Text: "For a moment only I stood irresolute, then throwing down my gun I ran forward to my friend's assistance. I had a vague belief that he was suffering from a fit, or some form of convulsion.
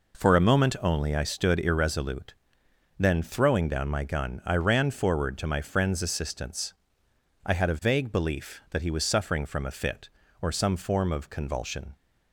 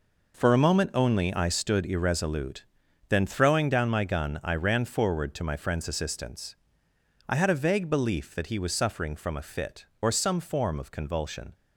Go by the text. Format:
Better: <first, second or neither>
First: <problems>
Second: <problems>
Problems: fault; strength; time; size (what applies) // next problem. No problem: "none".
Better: neither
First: none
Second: none